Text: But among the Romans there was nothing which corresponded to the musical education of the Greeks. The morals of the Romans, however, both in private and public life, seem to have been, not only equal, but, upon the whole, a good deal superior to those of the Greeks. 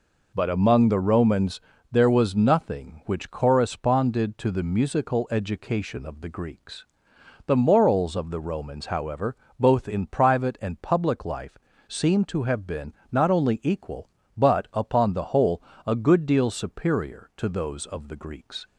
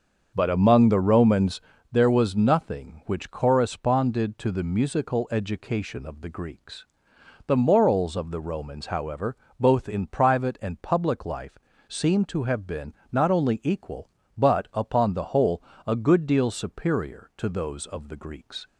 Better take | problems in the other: first | starts louder than the rest; until 1.9 s; 7 dB // pauses between "Romans" and "there"; slight; at 1.6 s; 0.30 s long; slight in the first

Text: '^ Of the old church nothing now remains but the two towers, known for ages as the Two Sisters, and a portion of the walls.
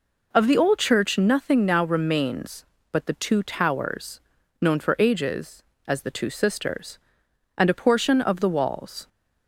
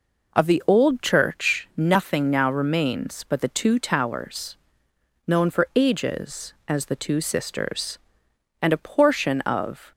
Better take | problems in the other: first | stops before "the walls"; at 9.9 s

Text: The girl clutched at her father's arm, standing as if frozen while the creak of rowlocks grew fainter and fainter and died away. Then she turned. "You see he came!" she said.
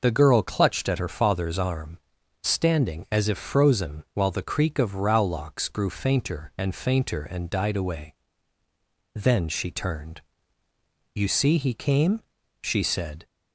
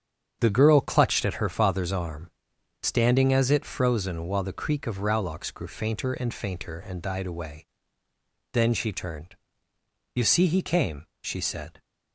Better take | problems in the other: first | starts louder than the rest; strong; until 1.4 s; 8 dB // says "it" for "if"; at 3.5 s

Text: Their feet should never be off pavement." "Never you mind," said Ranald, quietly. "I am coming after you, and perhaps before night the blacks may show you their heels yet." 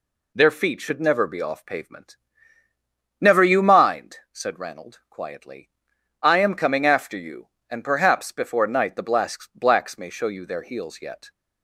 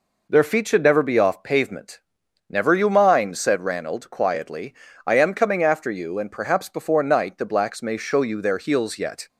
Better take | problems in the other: second | says "blacks" twice; at 9.5 s

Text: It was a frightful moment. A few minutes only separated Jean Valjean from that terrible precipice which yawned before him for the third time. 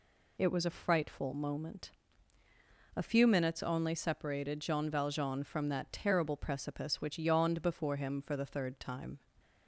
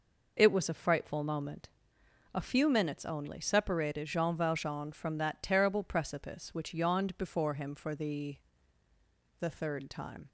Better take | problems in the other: first | says "the" twice; at 9.4 s

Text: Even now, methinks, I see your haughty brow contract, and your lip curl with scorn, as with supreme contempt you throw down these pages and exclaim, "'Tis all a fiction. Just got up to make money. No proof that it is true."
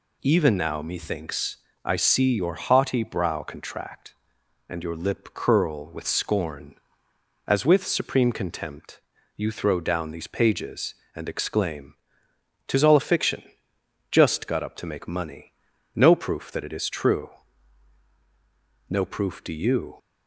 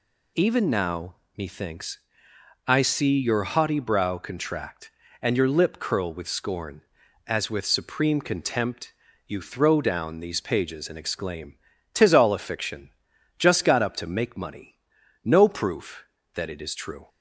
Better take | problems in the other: second | pauses between "contempt" and "you"; slight; at 8.9 s; 0.36 s long; slight in the second // goes on to say "No proof do you"; noticeable; from 18.8 s on; 1.0 s long

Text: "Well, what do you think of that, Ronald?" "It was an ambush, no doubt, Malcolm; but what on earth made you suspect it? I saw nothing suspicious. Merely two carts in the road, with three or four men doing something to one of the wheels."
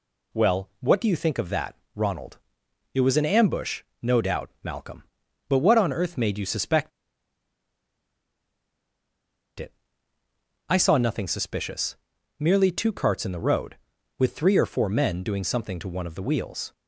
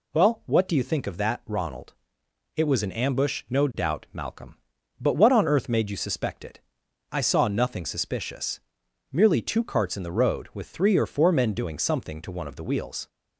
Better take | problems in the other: second | pauses between "suspect" and "it"; strong; at 6.9 s; 2.6 s long

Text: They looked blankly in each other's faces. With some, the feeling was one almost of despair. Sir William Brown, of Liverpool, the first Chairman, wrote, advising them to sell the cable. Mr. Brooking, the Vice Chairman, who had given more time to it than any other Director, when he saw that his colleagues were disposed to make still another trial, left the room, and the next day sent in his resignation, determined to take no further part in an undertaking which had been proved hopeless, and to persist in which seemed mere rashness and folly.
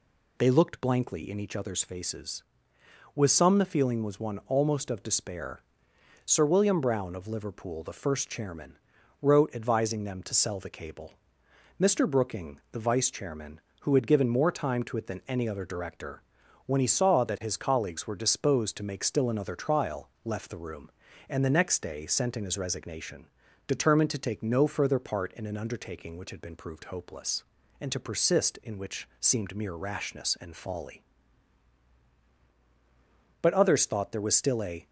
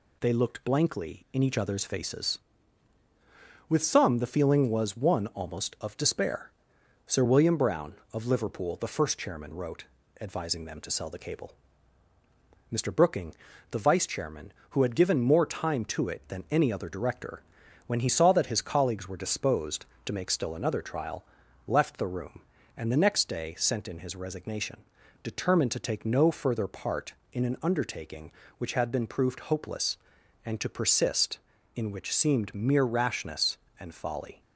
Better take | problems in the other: second | goes on to say "But others thought there was still a"; from 33.4 s on; 1.4 s long

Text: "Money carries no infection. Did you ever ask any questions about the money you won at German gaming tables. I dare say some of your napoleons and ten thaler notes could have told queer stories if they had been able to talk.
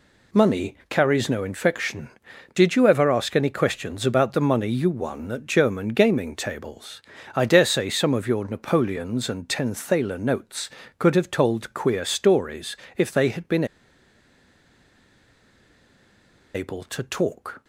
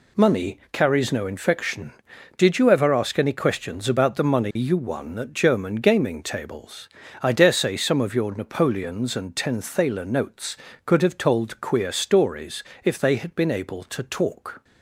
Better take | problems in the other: second | pauses between "stories" and "if"; slight; at 12.7 s; 0.20 s long; slight in the second // pauses between "been" and "able"; strong; at 13.6 s; 2.8 s long

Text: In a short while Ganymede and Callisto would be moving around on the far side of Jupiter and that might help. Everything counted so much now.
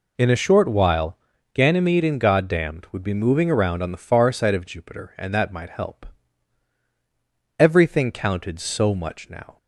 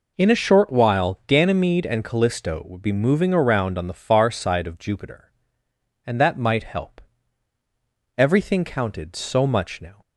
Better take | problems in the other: second | pauses between "while" and "Ganymede"; at 1.1 s; 0.38 s long // says "Goddamned" for "Callisto"; at 2.1 s

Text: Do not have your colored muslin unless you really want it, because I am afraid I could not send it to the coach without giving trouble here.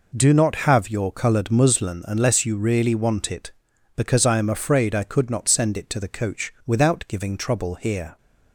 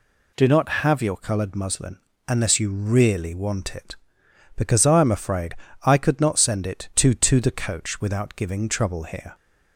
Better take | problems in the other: first | pauses between "muslin" and "unless"; slight; at 1.9 s; 0.28 s long // pauses between "afraid" and "I"; slight; at 5.5 s; 0.30 s long // says "to" twice; at 7.1 s

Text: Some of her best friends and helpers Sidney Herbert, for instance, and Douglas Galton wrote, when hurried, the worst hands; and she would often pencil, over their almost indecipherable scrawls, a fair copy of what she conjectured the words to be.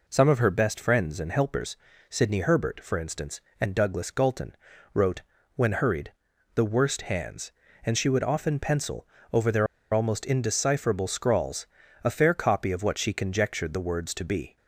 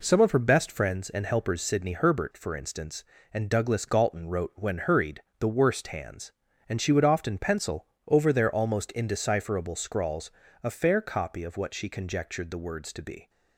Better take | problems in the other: second | pauses between "helpers" and "Sidney"; slight; at 1.7 s; 0.34 s long // pauses between "Galton" and "wrote"; at 4.5 s; 0.38 s long // pauses between "their" and "almost"; slight; at 9.6 s; 0.27 s long

